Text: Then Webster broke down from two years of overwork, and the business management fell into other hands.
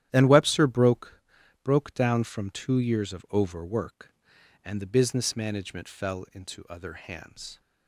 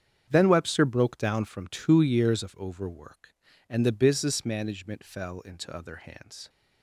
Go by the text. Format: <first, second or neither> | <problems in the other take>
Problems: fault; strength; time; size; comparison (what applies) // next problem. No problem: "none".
second | starts louder than the rest; strong; until 1.1 s; 11.5 dB; strong in the second // says "broke" twice; at 1.6 s